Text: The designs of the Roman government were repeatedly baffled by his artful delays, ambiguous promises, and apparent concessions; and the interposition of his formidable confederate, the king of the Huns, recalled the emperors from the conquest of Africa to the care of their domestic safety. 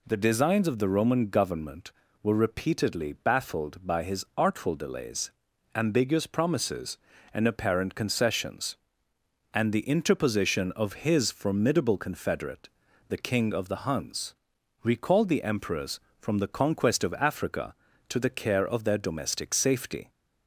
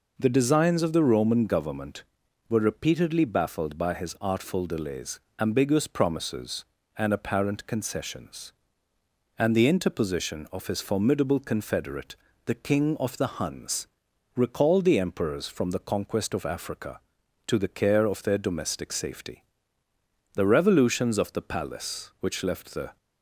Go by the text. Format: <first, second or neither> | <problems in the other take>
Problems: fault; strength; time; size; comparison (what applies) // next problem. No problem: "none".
first | goes on to say "The revolutions of the palace which left the"; strong; from 20.3 s on; 2.6 s long